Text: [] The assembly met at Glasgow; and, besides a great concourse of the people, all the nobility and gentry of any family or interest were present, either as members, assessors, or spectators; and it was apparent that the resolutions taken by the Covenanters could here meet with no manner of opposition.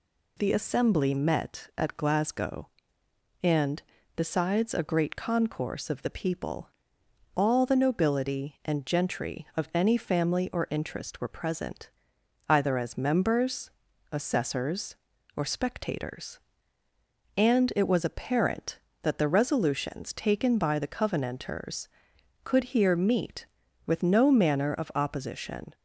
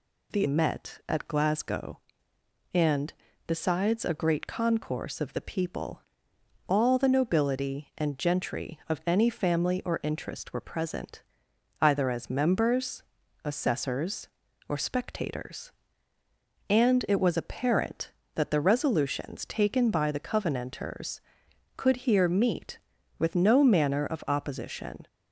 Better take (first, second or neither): first